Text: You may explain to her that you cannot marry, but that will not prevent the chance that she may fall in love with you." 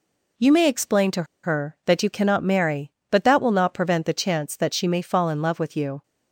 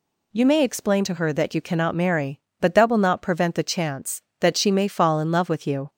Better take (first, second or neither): second